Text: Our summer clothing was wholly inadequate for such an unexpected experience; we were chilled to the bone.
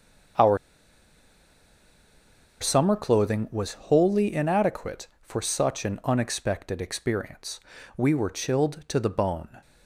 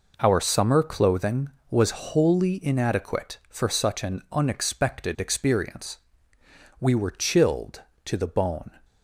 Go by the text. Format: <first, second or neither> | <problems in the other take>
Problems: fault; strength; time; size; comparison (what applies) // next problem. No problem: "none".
second | starts louder than the rest; until 3.4 s; 7 dB // pauses between "Our" and "summer"; strong; at 0.5 s; 2.0 s long